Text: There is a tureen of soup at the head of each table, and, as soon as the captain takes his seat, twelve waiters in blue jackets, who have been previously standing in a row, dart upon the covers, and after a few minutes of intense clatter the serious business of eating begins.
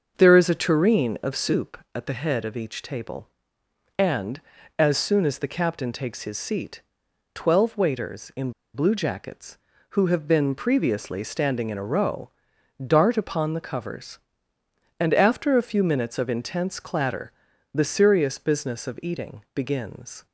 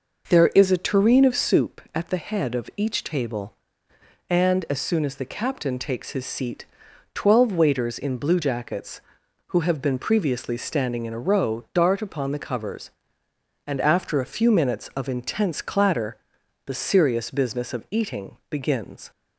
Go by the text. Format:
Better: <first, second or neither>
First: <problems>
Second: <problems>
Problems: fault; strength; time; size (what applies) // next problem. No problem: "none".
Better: second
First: starts louder than the rest; until 1.1 s; 6.5 dB // pauses between "in" and "blue"; slight; at 8.5 s; 0.21 s long // pauses between "clatter" and "the"; at 17.3 s; 0.42 s long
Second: pauses between "clatter" and "the"; noticeable; at 16.1 s; 0.48 s long